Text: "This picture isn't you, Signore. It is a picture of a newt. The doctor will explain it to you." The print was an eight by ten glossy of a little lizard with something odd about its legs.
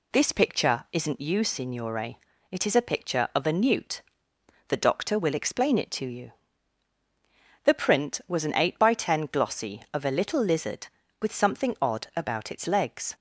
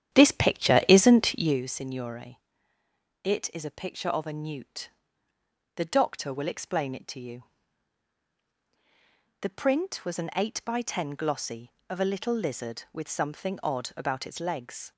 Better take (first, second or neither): first